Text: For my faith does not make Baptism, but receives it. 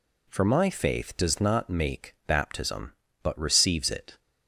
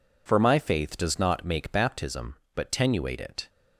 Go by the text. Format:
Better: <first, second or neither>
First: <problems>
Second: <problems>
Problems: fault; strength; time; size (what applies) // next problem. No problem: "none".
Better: first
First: none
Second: says "tenuate" for "receives"; at 2.7 s